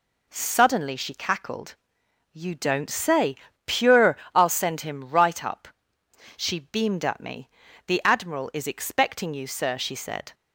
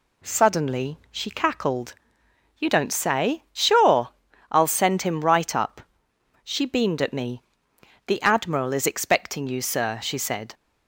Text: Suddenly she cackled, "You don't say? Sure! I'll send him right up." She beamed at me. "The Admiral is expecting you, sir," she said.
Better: second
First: says "Pure" for "Sure"; at 3.6 s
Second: none

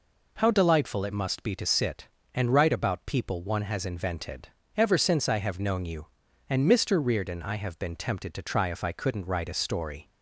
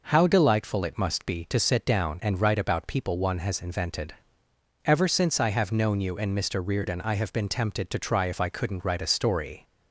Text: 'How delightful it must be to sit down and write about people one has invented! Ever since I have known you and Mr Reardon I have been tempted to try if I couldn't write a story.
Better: second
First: skips "down"; at 2.2 s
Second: none

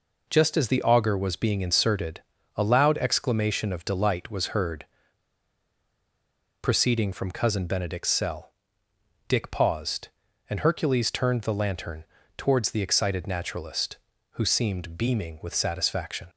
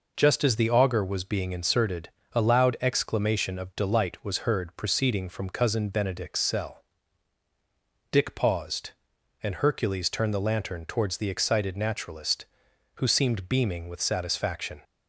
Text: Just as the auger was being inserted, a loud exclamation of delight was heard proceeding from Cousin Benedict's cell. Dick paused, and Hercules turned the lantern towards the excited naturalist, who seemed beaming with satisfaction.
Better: second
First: pauses between "heard" and "proceeding"; strong; at 4.8 s; 1.7 s long // pauses between "lantern" and "towards"; slight; at 12.0 s; 0.32 s long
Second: none

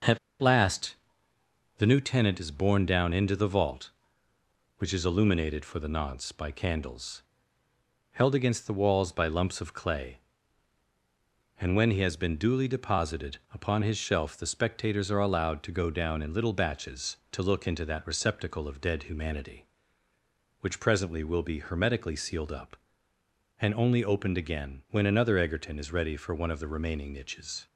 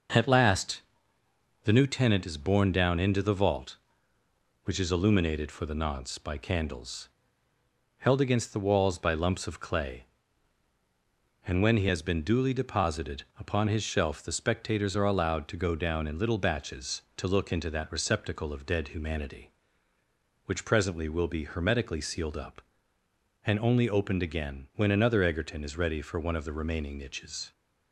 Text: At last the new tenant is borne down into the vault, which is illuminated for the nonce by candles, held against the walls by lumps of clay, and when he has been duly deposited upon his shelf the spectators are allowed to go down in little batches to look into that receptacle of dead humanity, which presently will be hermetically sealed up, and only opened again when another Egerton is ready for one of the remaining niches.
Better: second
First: pauses between "At" and "last"; slight; at 0.1 s; 0.22 s long // pauses between "last" and "the"; noticeable; at 0.9 s; 0.82 s long // pauses between "deposited" and "upon"; slight; at 13.3 s; 0.16 s long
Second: pauses between "last" and "the"; noticeable; at 0.8 s; 0.82 s long // pauses between "deposited" and "upon"; slight; at 13.2 s; 0.16 s long

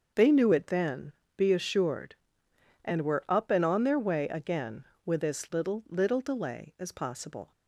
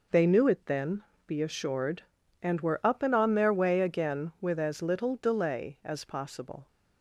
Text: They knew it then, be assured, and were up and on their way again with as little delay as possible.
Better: second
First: starts louder than the rest; until 1.4 s; 6.5 dB // says "little" twice; at 5.8 s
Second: none

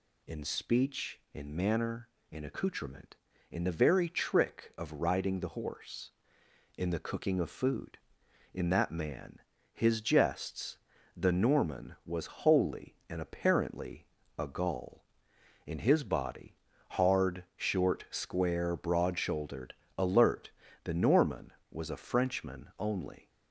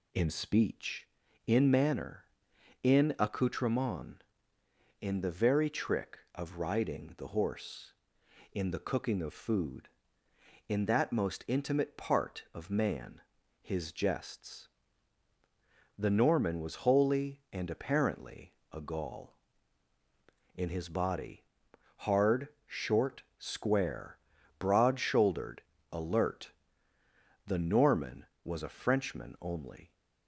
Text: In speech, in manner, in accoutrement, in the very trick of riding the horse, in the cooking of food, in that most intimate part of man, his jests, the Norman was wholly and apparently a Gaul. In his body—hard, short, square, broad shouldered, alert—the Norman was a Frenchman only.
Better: second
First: skips "most intimate part of"; at 8.9 s // pauses between "apparently" and "a"; slight; at 14.0 s; 0.32 s long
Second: pauses between "apparently" and "a"; slight; at 18.5 s; 0.20 s long

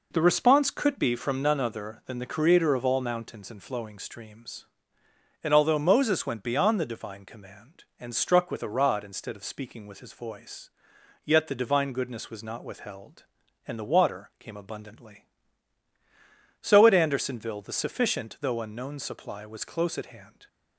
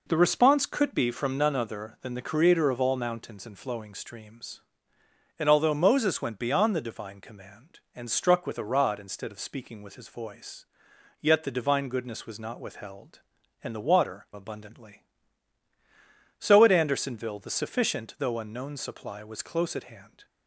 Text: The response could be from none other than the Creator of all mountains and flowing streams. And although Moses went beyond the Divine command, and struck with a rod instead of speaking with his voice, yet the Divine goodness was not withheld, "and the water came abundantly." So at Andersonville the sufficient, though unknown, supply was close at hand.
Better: first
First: none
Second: skips "came"; at 14.3 s

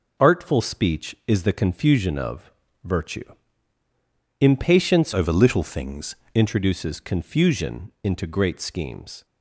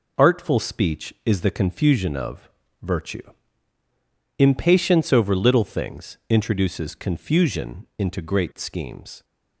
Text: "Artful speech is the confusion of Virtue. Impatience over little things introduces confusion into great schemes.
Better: second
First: pauses between "of" and "Virtue"; slight; at 2.5 s; 0.32 s long // changes voice from "over" to "things"; from 5.1 to 6.1 s; 1.0 s long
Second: pauses between "of" and "Virtue"; slight; at 2.4 s; 0.32 s long

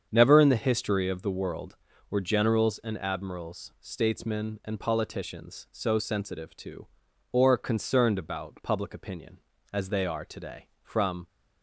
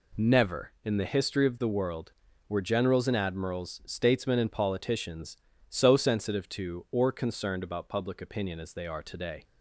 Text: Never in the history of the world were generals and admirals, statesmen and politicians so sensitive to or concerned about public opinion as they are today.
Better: second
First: starts louder than the rest; strong; until 1.1 s; 7.5 dB // goes on to say "From"; slight; from 10.8 s on; 0.44 s long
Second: none

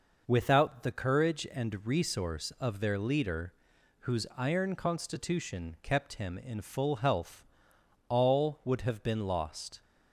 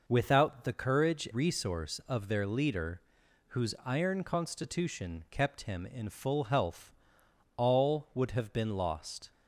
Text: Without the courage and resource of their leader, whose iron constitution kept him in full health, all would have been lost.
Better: first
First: none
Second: skips "and"; at 1.2 s

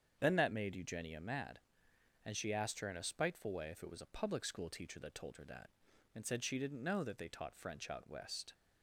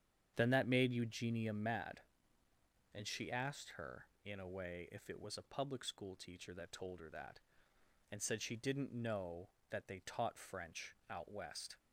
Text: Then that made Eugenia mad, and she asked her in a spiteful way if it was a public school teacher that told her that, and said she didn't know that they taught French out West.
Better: first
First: starts louder than the rest; strong; until 1.2 s; 7.5 dB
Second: starts louder than the rest; strong; until 1.3 s; 8.5 dB // skips "spiteful"; at 4.4 s

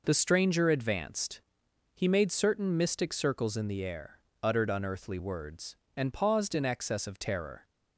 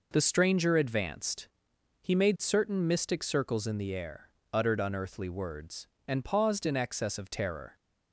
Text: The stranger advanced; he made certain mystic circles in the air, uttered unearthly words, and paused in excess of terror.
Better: neither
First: none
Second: none

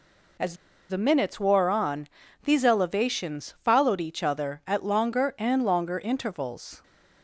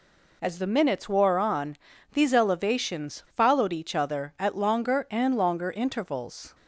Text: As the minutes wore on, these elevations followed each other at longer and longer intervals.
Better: second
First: pauses between "As" and "the"; slight; at 0.5 s; 0.34 s long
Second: none

